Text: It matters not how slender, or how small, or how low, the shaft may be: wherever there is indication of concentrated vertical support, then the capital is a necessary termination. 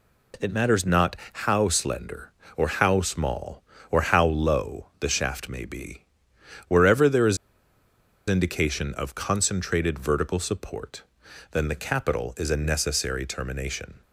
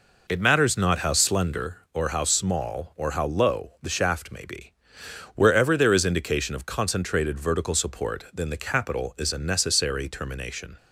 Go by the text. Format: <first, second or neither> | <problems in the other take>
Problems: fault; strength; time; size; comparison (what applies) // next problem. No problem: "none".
second | pauses between "not" and "how"; slight; at 1.1 s; 0.18 s long // pauses between "is" and "indication"; noticeable; at 7.3 s; 0.92 s long